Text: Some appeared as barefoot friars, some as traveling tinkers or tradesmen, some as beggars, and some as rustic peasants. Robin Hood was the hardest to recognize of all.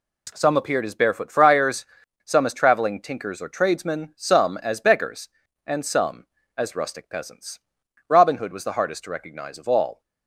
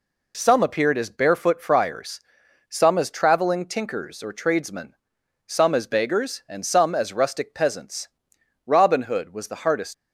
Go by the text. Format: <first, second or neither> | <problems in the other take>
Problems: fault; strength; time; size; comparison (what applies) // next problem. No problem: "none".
first | stops before "to recognize of all"; at 9.9 s